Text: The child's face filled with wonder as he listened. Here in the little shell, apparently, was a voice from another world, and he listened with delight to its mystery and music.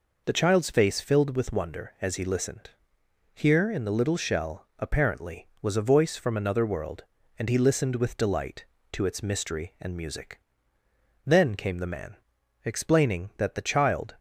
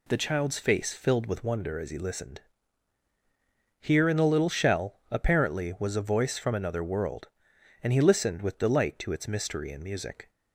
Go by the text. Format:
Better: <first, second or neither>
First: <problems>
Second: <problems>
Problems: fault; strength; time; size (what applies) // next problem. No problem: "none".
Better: second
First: goes on to say "Then came the man explaining that the child"; strong; from 11.2 s on; 2.9 s long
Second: none